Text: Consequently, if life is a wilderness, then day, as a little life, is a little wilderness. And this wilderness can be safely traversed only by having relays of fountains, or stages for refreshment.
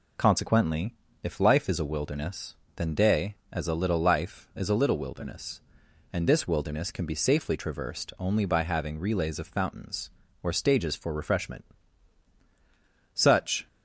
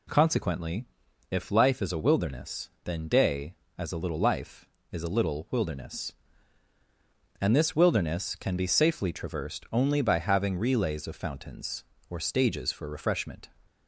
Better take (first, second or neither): second